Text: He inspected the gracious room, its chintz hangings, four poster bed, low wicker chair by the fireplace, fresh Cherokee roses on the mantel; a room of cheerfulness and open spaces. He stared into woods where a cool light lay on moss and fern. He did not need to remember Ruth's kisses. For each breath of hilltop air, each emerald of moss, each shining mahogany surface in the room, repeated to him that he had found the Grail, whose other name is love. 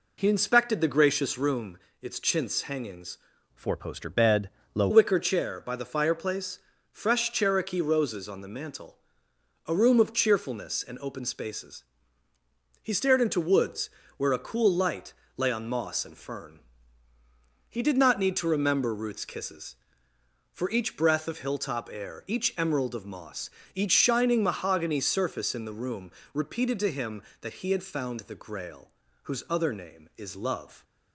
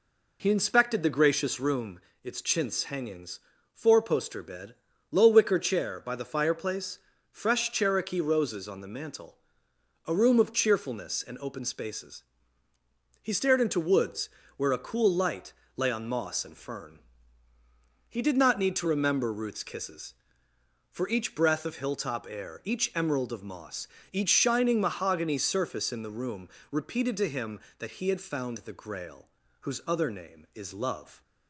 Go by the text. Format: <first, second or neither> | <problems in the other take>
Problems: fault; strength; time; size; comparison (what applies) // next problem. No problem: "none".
second | changes voice from "four" to "low"; from 3.5 to 4.8 s; 1.3 s long // pauses between "woods" and "where"; slight; at 13.9 s; 0.26 s long; slight in the second // pauses between "light" and "lay"; slight; at 15.1 s; 0.24 s long; slight in the second